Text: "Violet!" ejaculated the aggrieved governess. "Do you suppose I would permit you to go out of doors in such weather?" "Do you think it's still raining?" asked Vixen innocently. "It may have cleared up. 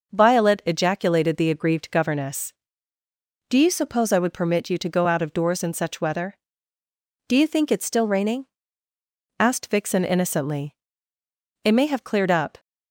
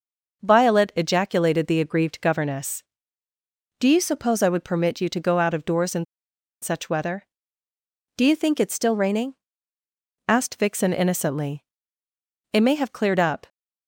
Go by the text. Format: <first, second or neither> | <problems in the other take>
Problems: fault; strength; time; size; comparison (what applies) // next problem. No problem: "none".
first | pauses between "in" and "such"; noticeable; at 6.0 s; 0.57 s long